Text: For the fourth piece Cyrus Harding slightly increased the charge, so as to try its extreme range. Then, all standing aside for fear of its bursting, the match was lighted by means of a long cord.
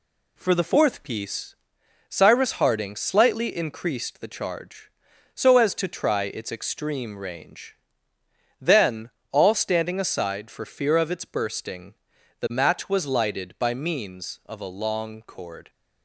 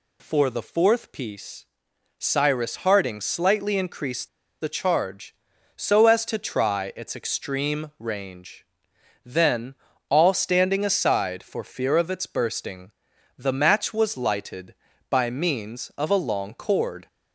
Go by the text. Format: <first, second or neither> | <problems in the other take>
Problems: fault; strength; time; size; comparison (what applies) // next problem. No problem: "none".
first | pauses between "piece" and "Cyrus"; noticeable; at 1.6 s; 0.54 s long; noticeable in the first // pauses between "increased" and "the"; slight; at 4.2 s; 0.32 s long